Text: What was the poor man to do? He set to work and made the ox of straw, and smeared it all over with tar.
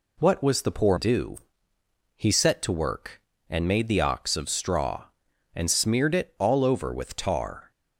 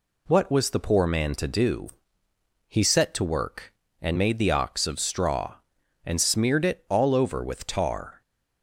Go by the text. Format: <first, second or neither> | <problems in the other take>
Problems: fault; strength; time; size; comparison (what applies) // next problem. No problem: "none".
second | skips "man to"; at 0.9 s